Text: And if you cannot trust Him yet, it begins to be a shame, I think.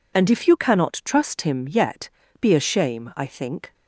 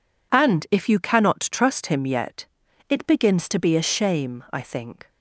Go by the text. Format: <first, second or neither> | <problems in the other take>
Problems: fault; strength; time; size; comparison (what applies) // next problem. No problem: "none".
second | skips "it begins to"; at 2.2 s